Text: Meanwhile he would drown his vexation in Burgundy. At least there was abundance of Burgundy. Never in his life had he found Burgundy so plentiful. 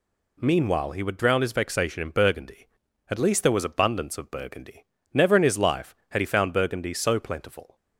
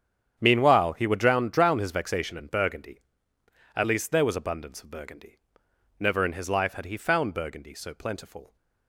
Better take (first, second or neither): first